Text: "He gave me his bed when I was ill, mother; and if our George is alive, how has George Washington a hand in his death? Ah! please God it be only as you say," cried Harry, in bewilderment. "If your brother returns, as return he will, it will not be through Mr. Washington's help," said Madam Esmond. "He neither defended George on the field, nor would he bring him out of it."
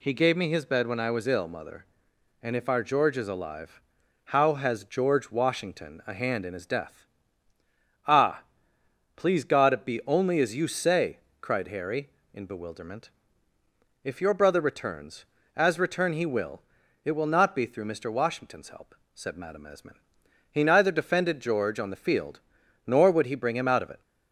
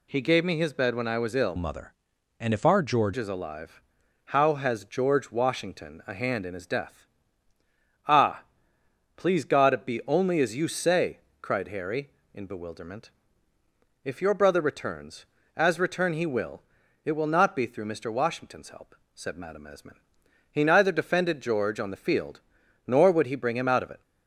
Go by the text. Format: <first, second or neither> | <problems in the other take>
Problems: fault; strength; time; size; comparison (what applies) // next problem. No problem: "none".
first | changes voice from "mother" to "George"; from 1.5 to 3.1 s; 1.6 s long